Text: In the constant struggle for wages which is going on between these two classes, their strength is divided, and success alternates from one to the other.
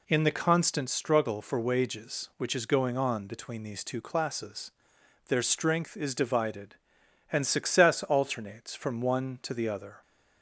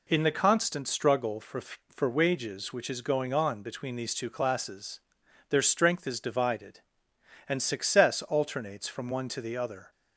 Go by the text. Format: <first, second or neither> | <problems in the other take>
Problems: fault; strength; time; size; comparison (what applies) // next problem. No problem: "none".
first | says "for" twice; at 1.5 s